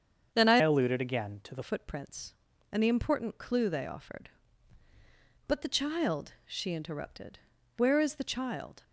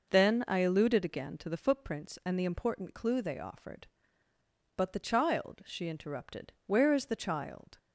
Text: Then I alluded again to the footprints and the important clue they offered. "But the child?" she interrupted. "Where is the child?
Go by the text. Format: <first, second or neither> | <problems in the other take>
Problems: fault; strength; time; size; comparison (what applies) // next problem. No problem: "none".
second | starts louder than the rest; strong; until 1.3 s; 7.5 dB // changes voice from "alluded" to "the"; from 0.6 to 1.6 s; 1.0 s long